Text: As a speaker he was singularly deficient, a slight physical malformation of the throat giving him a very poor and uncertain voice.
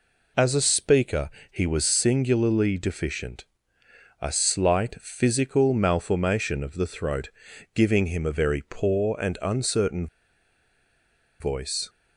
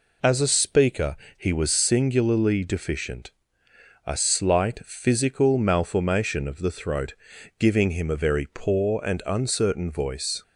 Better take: second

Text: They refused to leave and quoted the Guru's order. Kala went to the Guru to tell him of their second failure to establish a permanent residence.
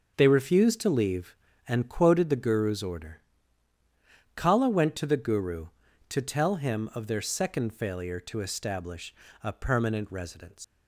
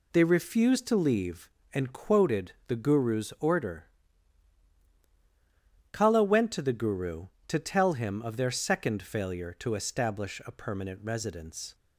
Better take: second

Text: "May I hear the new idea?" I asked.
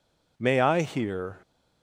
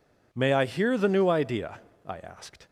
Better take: second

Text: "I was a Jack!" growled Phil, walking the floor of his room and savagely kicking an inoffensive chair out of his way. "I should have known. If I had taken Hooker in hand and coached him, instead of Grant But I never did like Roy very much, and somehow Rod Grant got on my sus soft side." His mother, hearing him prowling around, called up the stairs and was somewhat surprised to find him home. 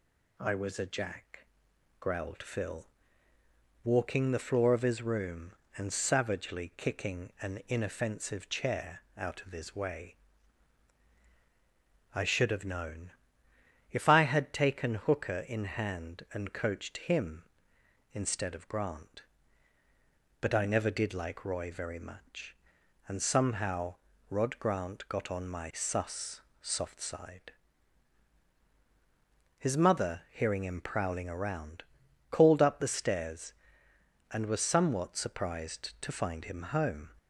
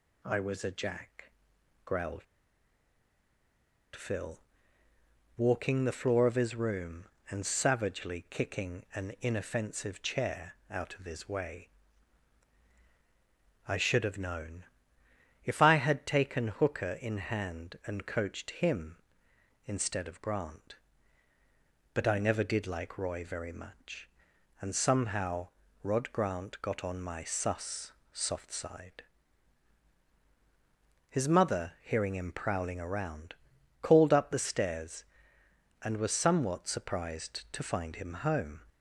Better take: first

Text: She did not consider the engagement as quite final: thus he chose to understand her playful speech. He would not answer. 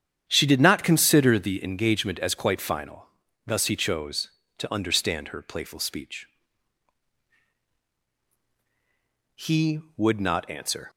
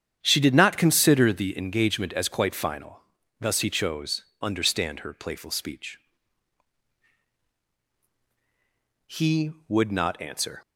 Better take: first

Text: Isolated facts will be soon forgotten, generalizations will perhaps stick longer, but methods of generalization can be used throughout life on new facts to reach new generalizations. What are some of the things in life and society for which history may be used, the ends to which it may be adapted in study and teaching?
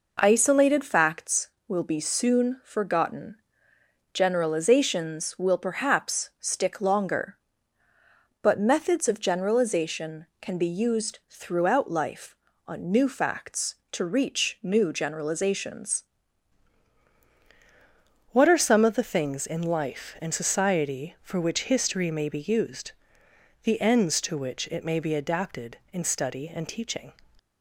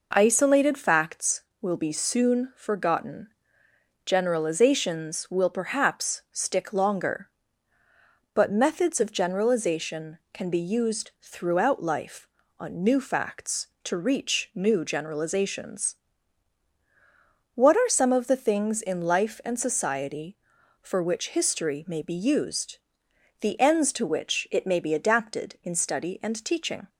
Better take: second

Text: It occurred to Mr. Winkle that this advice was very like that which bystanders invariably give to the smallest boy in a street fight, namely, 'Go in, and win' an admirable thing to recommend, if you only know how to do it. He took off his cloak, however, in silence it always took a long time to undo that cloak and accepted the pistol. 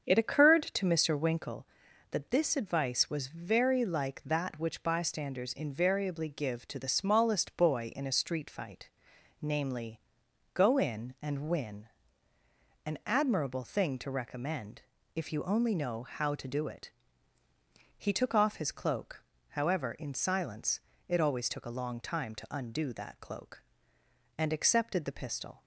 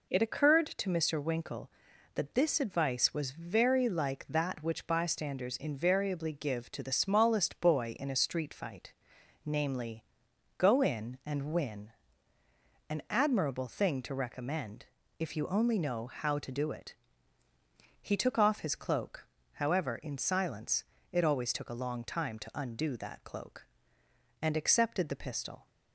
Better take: second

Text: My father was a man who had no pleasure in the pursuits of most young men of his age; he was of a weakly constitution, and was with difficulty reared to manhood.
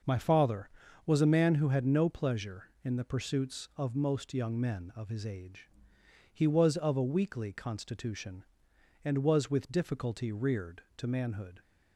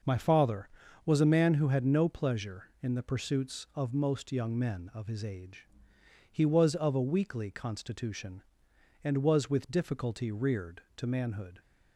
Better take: neither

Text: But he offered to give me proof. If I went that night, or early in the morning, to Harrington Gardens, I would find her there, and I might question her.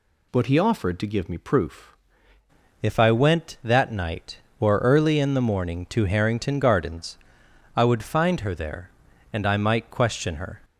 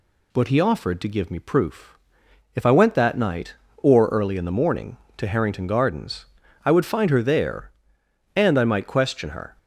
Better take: second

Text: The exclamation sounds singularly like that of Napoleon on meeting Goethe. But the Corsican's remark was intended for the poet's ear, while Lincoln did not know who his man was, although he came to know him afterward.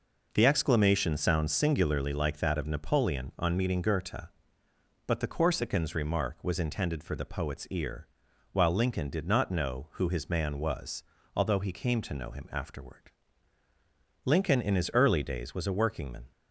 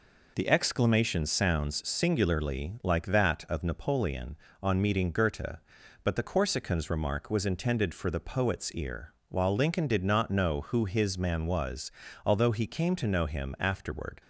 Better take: second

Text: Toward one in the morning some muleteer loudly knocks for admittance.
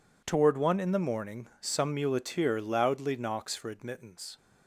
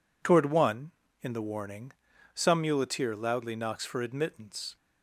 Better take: first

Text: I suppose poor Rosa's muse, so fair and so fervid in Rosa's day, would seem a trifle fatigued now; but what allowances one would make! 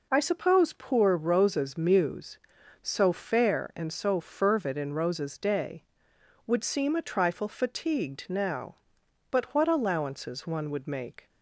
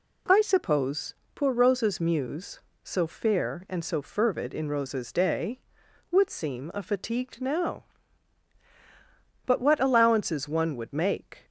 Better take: first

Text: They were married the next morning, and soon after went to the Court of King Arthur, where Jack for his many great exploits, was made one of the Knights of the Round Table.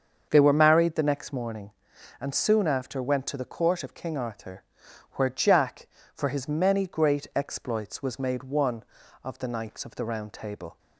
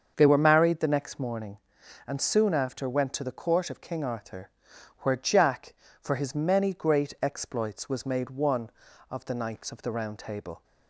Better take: neither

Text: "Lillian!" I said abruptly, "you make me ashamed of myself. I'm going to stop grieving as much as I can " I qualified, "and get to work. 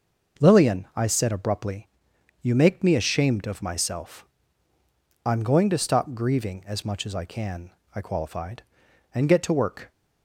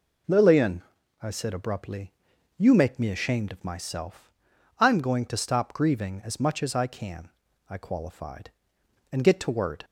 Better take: first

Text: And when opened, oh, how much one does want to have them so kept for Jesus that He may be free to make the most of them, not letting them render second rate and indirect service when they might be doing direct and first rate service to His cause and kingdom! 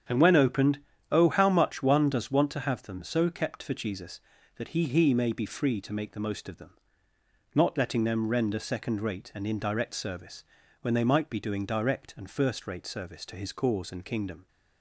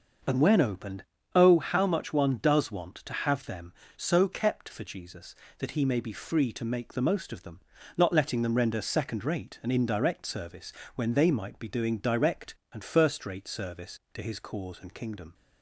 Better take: second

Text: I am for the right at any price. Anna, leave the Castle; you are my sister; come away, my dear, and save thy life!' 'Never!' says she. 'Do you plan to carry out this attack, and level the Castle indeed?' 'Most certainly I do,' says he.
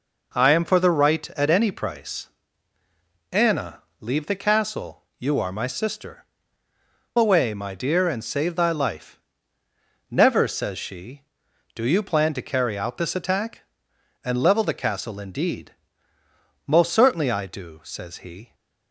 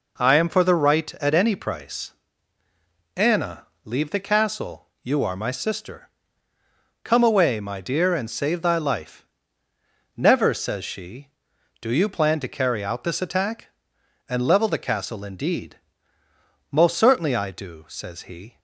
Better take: second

